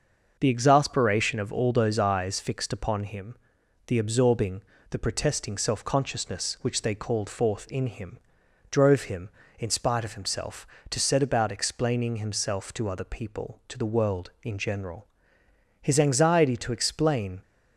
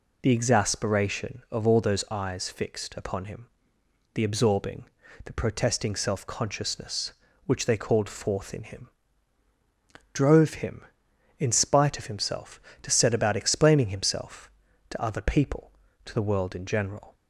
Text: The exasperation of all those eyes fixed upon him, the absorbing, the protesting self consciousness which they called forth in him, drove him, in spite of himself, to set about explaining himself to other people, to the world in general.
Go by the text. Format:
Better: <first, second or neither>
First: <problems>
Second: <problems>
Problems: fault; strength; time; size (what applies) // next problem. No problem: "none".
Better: second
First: starts louder than the rest; noticeable; until 1.4 s; 6 dB // goes on to say "His anxiety to explain"; from 15.8 s on; 1.6 s long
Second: none